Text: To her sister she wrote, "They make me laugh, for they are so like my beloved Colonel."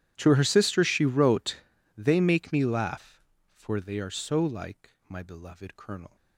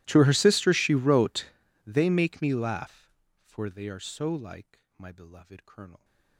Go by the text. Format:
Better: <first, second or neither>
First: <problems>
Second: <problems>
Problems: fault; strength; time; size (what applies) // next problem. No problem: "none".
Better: first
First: starts louder than the rest; strong; until 1.1 s; 11.5 dB // pauses between "like" and "my"; slight; at 4.9 s; 0.18 s long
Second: gets quieter; strong; throughout; 35 dB // starts louder than the rest; strong; until 1.0 s; 16.5 dB // pauses between "like" and "my"; slight; at 4.8 s; 0.18 s long